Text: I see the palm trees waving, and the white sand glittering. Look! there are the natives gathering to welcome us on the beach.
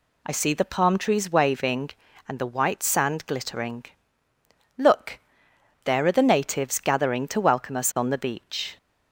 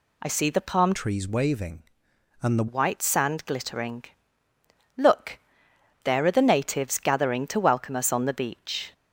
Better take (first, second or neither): first